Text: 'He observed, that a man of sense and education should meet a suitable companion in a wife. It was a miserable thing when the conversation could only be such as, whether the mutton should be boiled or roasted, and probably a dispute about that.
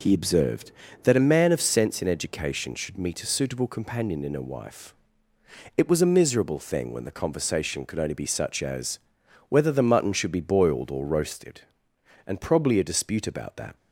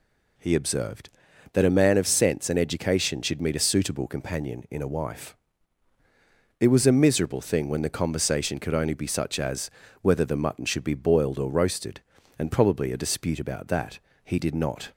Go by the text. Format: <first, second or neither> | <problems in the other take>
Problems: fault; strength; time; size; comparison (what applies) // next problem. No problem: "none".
first | goes on to say "He did not"; noticeable; from 14.2 s on; 0.68 s long